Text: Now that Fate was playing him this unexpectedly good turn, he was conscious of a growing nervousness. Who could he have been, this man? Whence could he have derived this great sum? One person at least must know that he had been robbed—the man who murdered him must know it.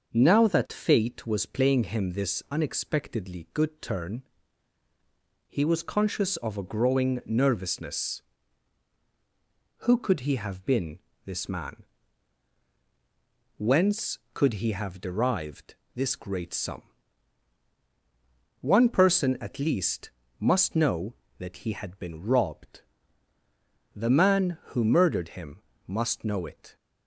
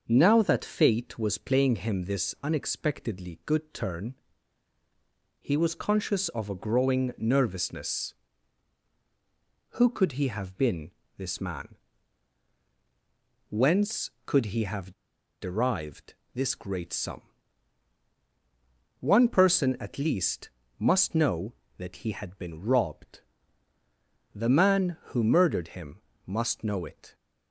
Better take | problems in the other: first | starts louder than the rest; until 1.0 s; 6.5 dB; also in the first // pauses between "have" and "derived"; noticeable; at 14.9 s; 0.47 s long // pauses between "derived" and "this"; slight; at 16.1 s; 0.22 s long; slight in the first // pauses between "least" and "must"; slight; at 20.5 s; 0.28 s long; slight in the first // pauses between "him" and "must"; slight; at 26.0 s; 0.26 s long; slight in the first

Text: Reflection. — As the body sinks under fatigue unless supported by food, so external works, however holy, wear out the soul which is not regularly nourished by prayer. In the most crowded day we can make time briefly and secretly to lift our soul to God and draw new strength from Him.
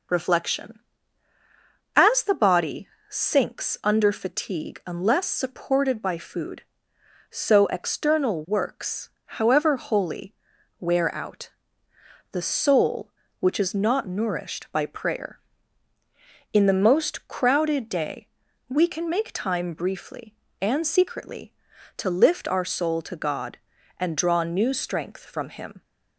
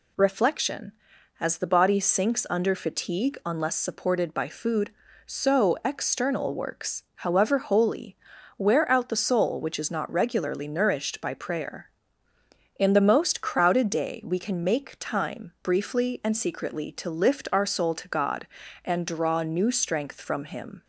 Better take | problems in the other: second | pauses between "body" and "sinks"; slight; at 2.8 s; 0.22 s long // pauses between "out" and "the"; noticeable; at 11.4 s; 0.82 s long // skips "regularly"; at 14.0 s // pauses between "day" and "we"; at 18.2 s; 0.42 s long

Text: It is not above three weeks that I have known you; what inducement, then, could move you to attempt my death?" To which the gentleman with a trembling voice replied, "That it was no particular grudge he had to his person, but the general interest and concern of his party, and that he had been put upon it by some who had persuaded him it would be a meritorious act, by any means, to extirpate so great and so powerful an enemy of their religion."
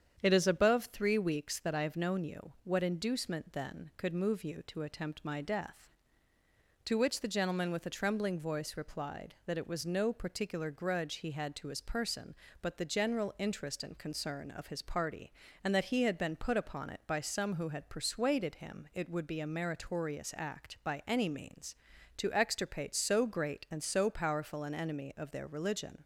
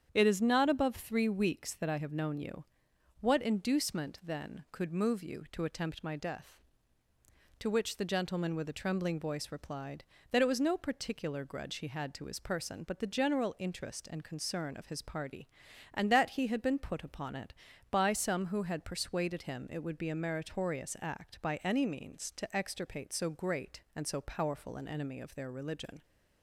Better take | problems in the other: second | starts louder than the rest; strong; until 1.2 s; 8 dB; strong in the second // skips "not"; at 0.4 s

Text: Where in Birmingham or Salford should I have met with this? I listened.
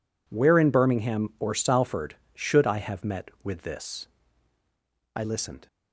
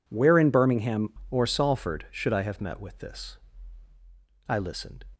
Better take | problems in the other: first | changes voice at "or"; from 1.3 s on; 3.7 s long

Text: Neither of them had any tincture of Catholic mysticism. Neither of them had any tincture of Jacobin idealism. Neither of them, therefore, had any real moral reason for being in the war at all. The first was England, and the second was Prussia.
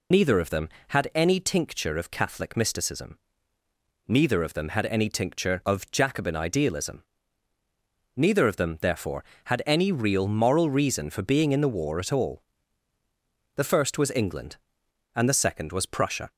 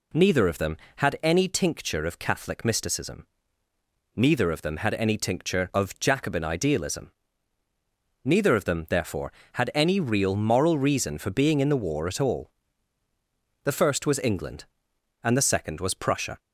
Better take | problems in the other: second | loses the start of "Neither"; at 0.1 s; 55 ms

